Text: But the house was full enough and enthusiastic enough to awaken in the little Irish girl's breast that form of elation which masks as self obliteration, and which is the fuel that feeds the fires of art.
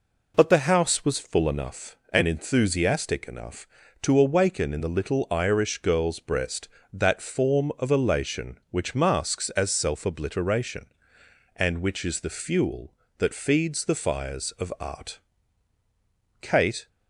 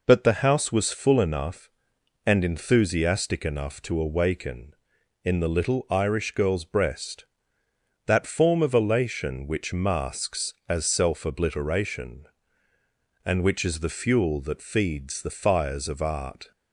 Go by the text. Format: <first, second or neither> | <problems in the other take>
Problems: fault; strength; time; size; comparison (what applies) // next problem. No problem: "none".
second | goes on to say "Kate"; slight; from 16.4 s on; 0.46 s long